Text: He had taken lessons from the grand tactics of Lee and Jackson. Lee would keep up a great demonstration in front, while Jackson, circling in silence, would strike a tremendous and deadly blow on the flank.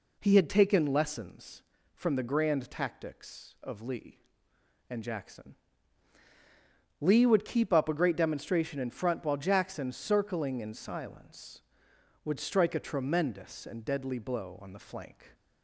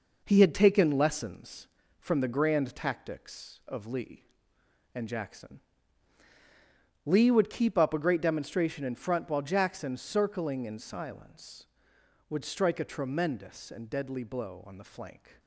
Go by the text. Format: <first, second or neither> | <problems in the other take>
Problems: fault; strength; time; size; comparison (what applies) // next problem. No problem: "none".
first | gets quieter; noticeable; throughout; 6 dB